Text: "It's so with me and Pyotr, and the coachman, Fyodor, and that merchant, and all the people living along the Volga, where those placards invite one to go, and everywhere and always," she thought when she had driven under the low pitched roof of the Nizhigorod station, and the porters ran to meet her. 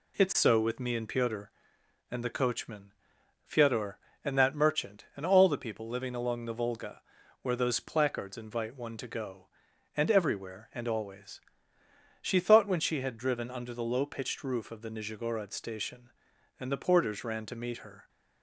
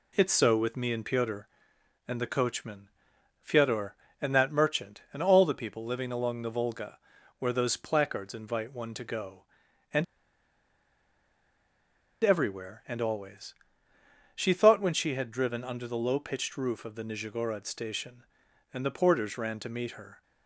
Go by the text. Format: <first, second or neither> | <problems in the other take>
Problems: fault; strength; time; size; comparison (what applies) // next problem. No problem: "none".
first | pauses between "and" and "everywhere"; strong; at 10.0 s; 2.1 s long